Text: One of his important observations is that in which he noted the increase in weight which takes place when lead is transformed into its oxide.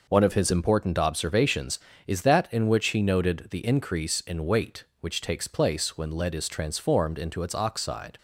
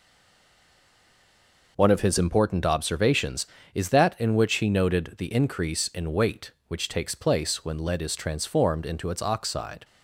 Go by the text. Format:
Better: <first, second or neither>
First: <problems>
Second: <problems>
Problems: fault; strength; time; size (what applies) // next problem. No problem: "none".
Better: first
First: none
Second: stays silent before the first word; noticeable; until 1.7 s; 1.7 s long